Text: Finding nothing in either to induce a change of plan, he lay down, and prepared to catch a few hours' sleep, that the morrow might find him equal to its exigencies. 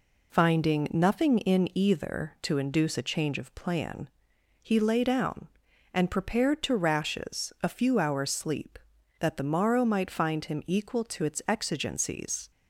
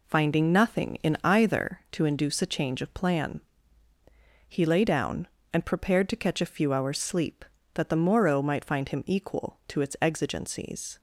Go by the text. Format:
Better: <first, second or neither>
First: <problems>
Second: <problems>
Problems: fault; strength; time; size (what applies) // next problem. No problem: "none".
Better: second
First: says "rashes" for "catch"; at 6.7 s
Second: none